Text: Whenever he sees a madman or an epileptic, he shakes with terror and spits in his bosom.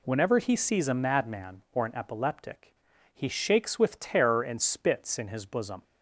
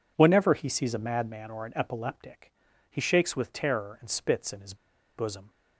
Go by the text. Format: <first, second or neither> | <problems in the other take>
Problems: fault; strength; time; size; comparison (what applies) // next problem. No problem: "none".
first | pauses between "his" and "bosom"; at 4.7 s; 0.42 s long